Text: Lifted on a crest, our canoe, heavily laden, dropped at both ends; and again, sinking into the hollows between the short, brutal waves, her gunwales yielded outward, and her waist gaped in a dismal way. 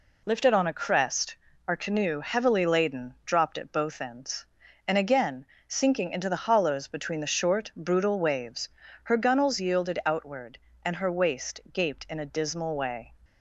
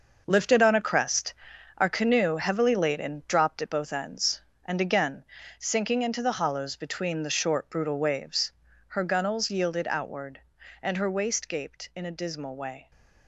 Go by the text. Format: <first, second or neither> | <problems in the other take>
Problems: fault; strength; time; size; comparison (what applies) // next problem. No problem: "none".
first | gets quieter; strong; throughout; 10 dB